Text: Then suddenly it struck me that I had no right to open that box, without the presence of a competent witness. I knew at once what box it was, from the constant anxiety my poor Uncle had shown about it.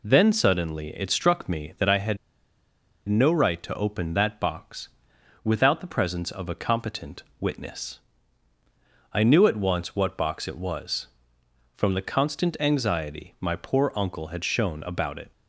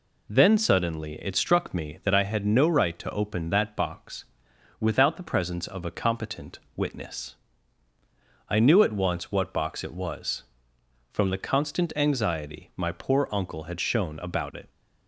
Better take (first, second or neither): second